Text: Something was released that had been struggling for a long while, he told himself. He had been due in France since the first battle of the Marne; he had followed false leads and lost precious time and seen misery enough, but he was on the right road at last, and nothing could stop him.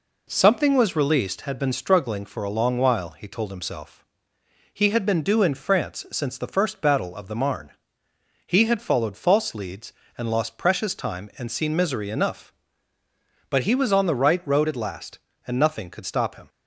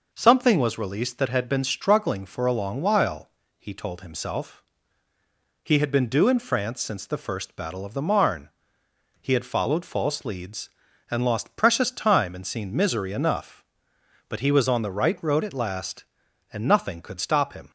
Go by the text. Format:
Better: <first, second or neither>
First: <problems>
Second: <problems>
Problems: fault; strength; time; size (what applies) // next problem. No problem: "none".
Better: second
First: skips "that"; at 1.4 s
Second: none